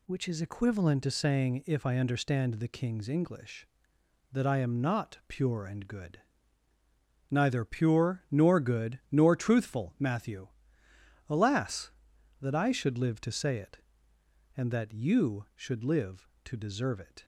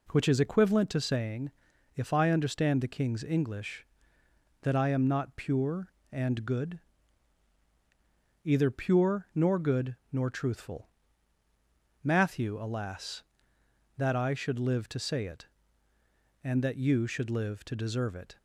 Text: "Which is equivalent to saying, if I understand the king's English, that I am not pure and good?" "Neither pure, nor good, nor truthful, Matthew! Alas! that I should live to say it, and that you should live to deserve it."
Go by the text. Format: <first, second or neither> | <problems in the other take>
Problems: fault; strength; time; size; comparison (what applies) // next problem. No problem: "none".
first | says "Either" for "Neither"; at 8.4 s